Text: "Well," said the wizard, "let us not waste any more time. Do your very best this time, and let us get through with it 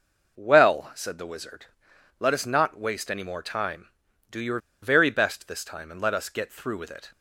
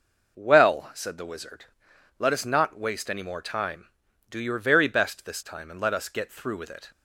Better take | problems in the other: second | pauses between "your" and "very"; slight; at 4.5 s; 0.22 s long

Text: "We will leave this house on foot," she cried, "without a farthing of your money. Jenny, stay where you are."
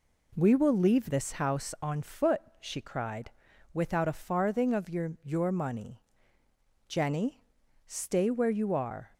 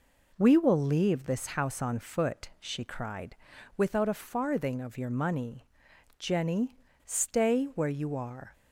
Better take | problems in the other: second | says "your" twice; at 5.2 s

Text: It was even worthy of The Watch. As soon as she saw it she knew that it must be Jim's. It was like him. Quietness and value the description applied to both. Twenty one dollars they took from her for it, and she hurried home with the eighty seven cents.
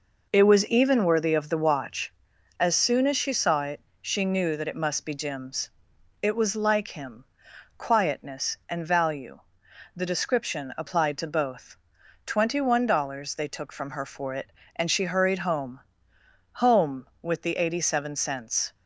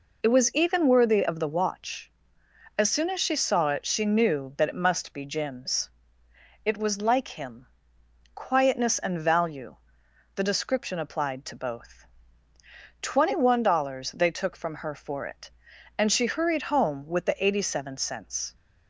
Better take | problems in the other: second | pauses between "it" and "she"; slight; at 3.8 s; 0.22 s long // pauses between "value" and "the"; noticeable; at 9.4 s; 0.56 s long; noticeable in the second // says "home" twice; at 16.5 s

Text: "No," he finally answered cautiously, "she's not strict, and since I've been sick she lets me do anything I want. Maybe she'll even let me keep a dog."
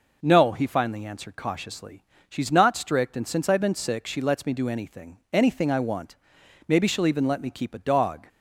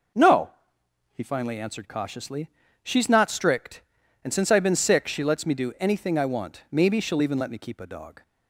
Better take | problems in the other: second | says "anything" twice; at 5.3 s

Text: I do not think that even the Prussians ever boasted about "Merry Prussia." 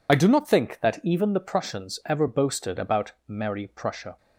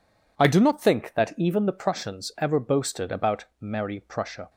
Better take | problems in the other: second | loses the start of "I"; at 0.0 s; 45 ms // pauses between "about" and "Merry"; slight; at 3.1 s; 0.16 s long; slight in the second

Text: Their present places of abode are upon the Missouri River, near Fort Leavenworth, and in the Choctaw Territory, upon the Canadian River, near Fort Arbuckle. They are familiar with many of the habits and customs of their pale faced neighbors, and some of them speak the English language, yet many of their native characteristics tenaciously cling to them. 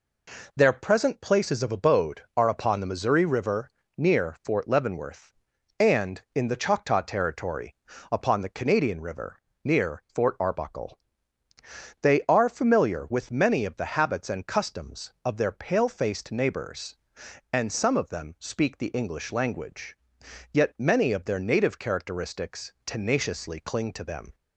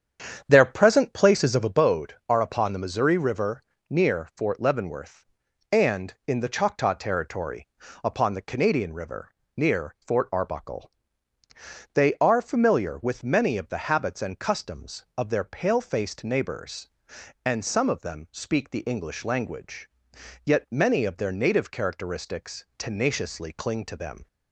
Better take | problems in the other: first | starts louder than the rest; strong; until 1.8 s; 8 dB

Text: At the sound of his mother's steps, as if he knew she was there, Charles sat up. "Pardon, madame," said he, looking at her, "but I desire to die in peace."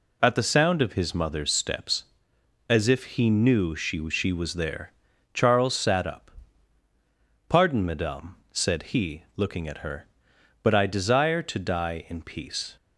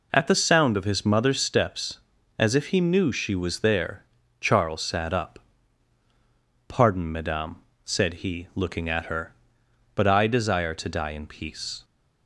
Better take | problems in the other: second | says "she" twice; at 4.0 s

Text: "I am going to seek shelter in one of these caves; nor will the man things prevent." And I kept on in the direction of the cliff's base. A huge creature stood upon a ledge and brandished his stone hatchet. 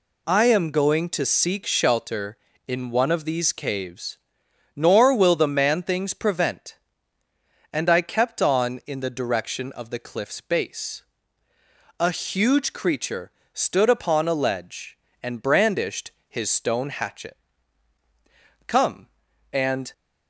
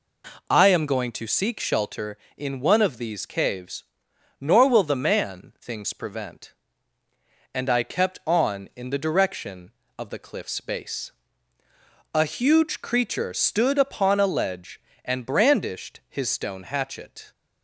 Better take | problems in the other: second | pauses between "creature" and "stood"; slight; at 13.3 s; 0.20 s long // pauses between "brandished" and "his"; slight; at 16.1 s; 0.16 s long // goes on to say "Come and"; noticeable; from 18.6 s on; 1.2 s long

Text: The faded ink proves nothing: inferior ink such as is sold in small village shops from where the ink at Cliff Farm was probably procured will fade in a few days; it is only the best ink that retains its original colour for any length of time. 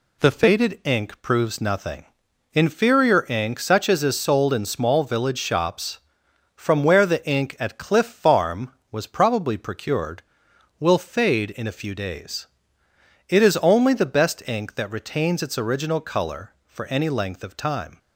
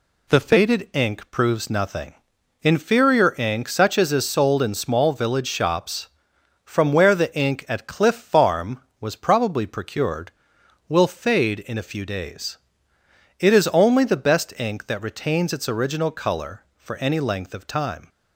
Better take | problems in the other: neither | none

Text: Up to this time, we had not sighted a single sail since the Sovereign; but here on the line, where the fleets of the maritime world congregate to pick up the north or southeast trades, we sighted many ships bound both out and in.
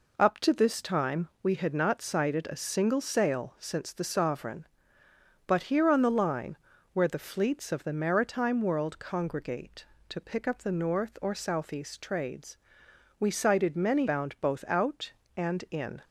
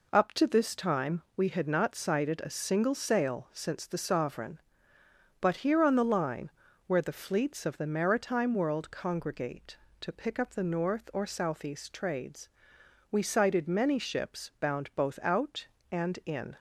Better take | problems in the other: second | skips "ships"; at 14.0 s

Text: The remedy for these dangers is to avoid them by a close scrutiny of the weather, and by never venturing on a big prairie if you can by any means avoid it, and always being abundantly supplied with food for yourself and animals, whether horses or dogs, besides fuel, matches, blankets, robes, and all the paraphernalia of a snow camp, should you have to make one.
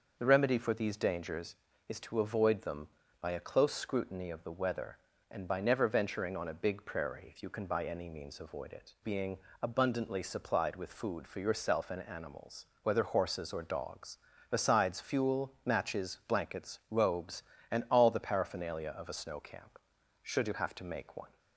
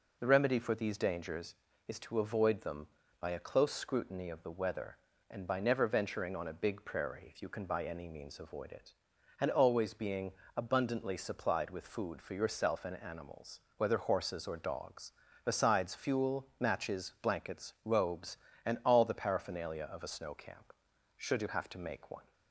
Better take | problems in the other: second | starts louder than the rest; until 1.2 s; 6.5 dB // skips "and always"; at 8.9 s // pauses between "being" and "abundantly"; slight; at 9.3 s; 0.24 s long; slight in the second

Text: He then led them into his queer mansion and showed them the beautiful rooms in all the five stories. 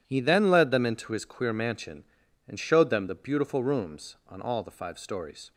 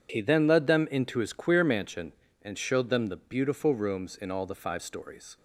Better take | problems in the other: second | says "on" for "in"; at 4.2 s

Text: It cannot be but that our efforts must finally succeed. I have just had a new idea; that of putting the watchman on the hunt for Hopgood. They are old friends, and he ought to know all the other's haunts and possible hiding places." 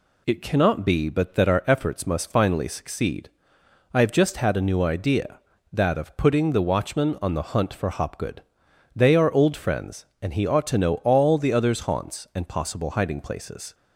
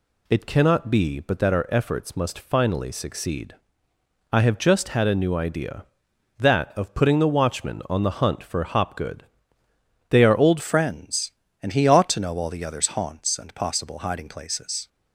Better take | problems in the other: first | changes voice at "friends"; from 10.5 s on; 4.3 s long

